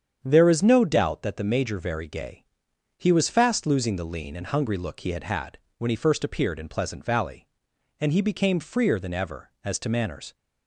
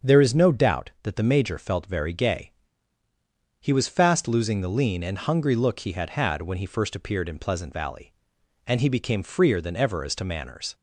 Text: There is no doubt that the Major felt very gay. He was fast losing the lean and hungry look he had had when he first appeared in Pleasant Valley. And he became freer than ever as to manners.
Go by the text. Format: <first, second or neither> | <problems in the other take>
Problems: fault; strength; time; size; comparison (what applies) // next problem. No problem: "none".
second | starts louder than the rest; strong; until 1.2 s; 8 dB; strong in the second // skips "felt"; at 1.7 s // pauses between "had" and "when"; slight; at 5.5 s; 0.20 s long